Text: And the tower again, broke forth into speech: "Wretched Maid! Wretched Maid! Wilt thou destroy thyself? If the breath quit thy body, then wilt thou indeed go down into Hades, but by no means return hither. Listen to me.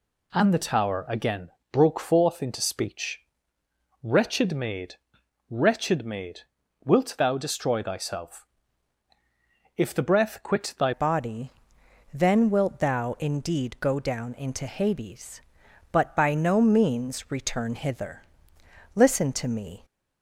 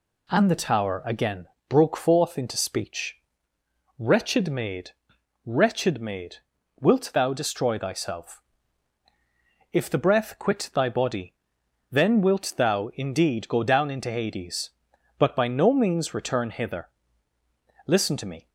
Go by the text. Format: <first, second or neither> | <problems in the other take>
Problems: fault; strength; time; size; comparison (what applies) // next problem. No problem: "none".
second | changes voice at "body"; from 10.9 s on; 8.9 s long